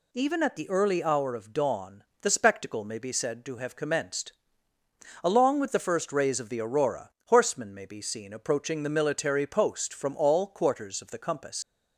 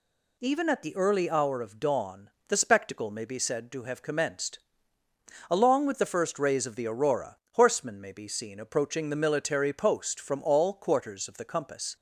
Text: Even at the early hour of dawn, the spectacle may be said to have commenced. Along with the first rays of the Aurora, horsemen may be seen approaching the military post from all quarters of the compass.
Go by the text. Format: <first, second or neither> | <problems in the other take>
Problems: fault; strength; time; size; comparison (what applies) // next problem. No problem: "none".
second | leaves "compass" unfinished; at 11.6 s; 65 ms